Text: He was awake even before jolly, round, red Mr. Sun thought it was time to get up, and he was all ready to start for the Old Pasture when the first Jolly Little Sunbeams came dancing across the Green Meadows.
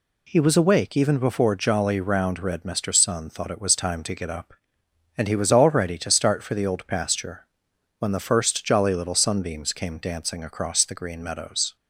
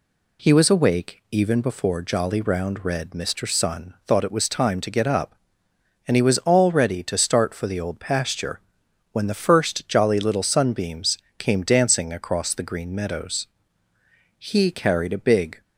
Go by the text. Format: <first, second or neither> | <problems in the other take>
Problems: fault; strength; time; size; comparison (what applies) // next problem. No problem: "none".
first | pauses between "Pasture" and "when"; noticeable; at 8.5 s; 0.54 s long; noticeable in the first // pauses between "Sunbeams" and "came"; slight; at 11.1 s; 0.18 s long // goes on to say "He carried a big"; noticeable; from 14.3 s on; 1.2 s long